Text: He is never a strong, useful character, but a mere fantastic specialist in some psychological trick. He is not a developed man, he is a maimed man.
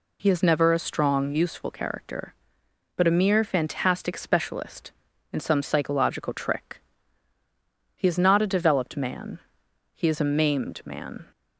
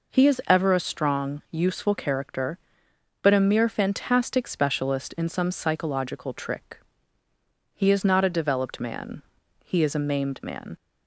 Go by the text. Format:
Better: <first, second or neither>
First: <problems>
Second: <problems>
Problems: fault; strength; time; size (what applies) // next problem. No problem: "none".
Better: first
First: none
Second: says "ever" for "never"; at 0.4 s